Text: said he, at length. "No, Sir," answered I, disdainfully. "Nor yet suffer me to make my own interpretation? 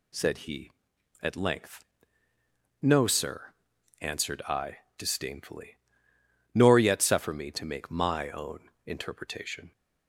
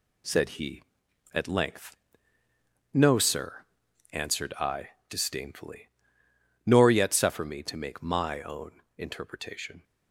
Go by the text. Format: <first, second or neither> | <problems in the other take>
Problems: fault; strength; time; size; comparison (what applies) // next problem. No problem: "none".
first | gets quieter; throughout; 7 dB // pauses between "own" and "interpretation"; slight; at 8.8 s; 0.16 s long; slight in the first